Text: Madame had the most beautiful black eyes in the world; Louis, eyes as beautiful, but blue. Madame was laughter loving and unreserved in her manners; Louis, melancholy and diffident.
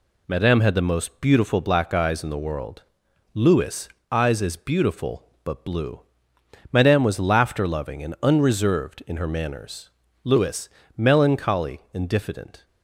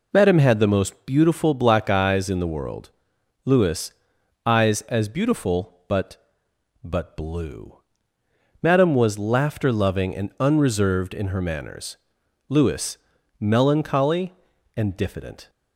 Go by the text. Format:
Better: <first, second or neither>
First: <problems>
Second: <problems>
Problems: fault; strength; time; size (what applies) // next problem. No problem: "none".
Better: first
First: none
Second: says "but" twice; at 6.8 s